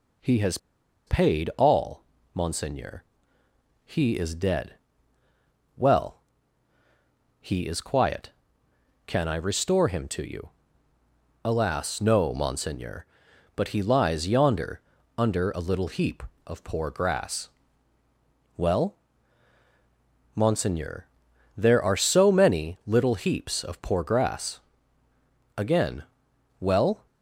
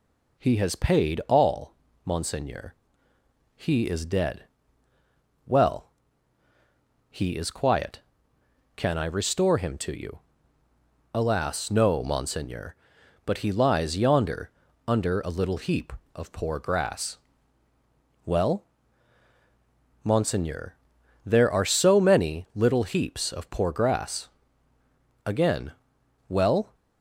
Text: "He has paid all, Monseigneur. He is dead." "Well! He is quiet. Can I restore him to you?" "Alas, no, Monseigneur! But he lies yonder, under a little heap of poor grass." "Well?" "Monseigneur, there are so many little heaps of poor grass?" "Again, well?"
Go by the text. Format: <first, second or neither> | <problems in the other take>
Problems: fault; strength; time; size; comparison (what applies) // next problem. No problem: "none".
second | pauses between "has" and "paid"; noticeable; at 0.5 s; 0.49 s long